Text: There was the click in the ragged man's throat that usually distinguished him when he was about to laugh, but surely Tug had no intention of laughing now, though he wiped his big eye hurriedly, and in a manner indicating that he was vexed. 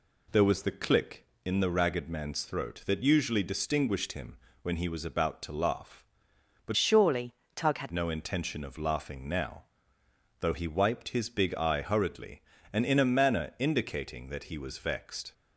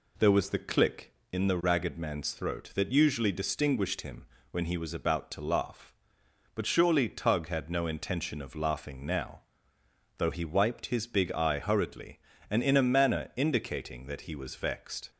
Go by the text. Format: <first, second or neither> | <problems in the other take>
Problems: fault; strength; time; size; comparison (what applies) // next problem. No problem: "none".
second | pauses between "him" and "when"; slight; at 4.3 s; 0.24 s long; slight in the second // changes voice from "surely" to "had"; from 6.7 to 7.9 s; 1.2 s long // pauses between "surely" and "Tug"; slight; at 7.3 s; 0.24 s long